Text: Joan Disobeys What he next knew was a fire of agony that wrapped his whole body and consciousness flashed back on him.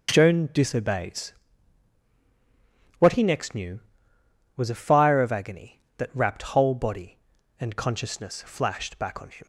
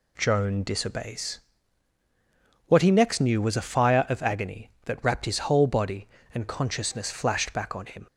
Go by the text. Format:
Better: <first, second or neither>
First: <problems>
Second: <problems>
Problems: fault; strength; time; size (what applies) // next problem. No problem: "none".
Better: second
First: pauses between "Disobeys" and "What"; strong; at 1.3 s; 1.6 s long // skips "his"; at 6.4 s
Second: pauses between "Disobeys" and "What"; strong; at 1.4 s; 1.2 s long